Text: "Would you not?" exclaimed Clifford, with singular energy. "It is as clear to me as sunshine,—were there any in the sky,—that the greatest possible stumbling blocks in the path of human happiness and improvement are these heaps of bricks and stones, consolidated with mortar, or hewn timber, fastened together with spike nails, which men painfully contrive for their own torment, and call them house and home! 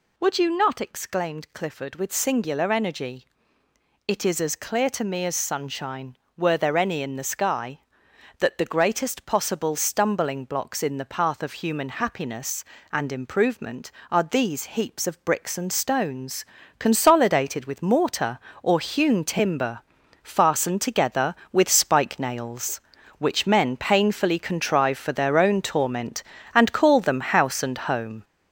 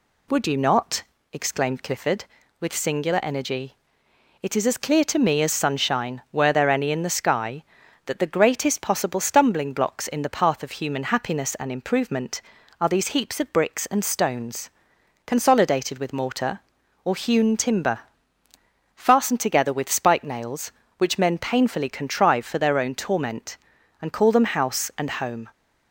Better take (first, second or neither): second